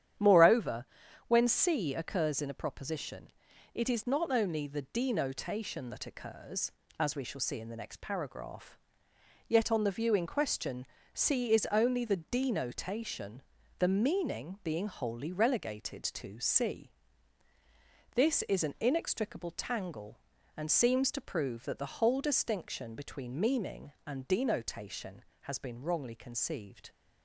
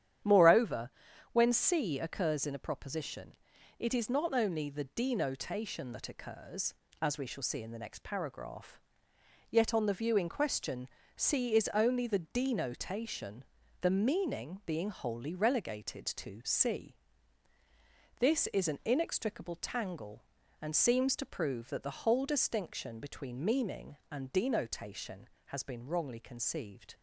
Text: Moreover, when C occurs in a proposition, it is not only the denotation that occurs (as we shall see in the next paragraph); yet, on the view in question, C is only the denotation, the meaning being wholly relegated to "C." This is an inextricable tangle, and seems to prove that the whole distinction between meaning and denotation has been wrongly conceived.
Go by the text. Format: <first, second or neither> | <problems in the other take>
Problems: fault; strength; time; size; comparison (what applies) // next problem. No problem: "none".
neither | starts louder than the rest; strong; the same in both